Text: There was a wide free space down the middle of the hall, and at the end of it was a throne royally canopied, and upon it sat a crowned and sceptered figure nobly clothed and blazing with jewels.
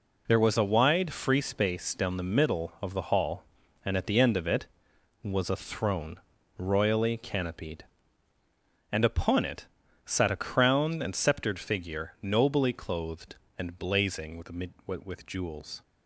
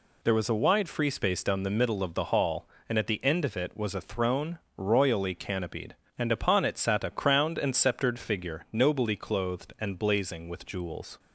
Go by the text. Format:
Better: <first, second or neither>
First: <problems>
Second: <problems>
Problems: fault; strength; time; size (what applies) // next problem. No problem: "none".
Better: second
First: pauses between "throne" and "royally"; at 6.1 s; 0.38 s long // pauses between "it" and "sat"; at 9.6 s; 0.40 s long // says "with" twice; at 15.0 s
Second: pauses between "throne" and "royally"; slight; at 4.5 s; 0.18 s long